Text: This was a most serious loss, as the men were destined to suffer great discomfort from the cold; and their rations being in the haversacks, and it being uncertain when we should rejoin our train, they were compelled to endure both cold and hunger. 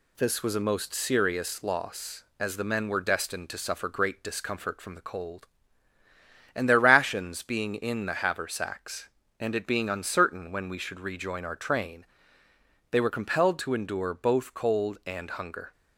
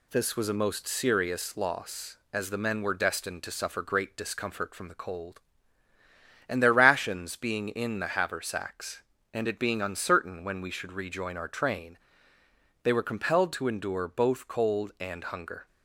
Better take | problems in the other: neither | none

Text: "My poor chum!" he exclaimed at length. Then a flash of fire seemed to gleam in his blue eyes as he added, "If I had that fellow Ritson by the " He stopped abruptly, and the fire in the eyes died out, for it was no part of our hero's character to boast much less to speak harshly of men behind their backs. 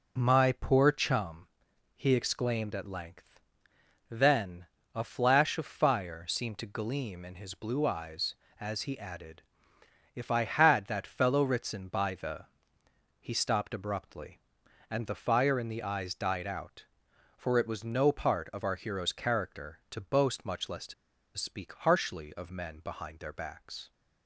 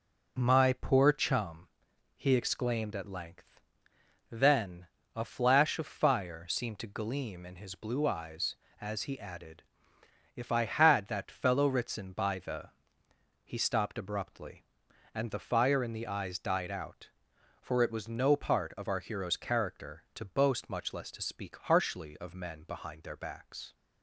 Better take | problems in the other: second | pauses between "Then" and "a"; slight; at 4.6 s; 0.30 s long; slight in the second // pauses between "to" and "speak"; at 20.9 s; 0.43 s long

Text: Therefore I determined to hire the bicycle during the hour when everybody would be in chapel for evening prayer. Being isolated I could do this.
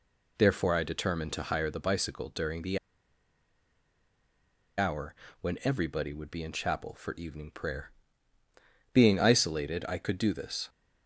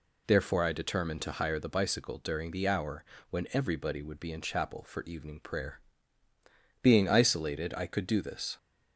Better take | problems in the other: second | pauses between "the" and "hour"; strong; at 2.7 s; 2.0 s long // pauses between "hour" and "when"; slight; at 5.1 s; 0.26 s long; slight in the second

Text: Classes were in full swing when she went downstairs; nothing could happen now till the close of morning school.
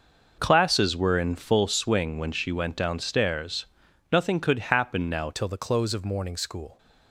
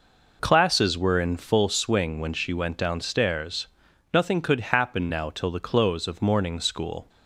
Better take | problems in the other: second | changes voice at "till"; from 5.3 s on; 1.4 s long

